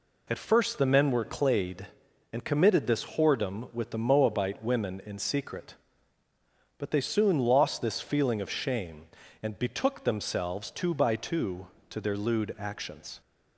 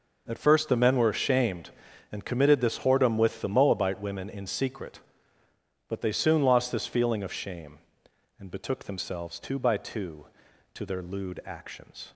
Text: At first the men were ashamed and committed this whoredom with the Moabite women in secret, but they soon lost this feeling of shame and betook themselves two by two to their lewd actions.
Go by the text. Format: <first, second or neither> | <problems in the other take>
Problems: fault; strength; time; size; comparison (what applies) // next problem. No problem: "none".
second | says "clayed" for "ashamed"; at 1.2 s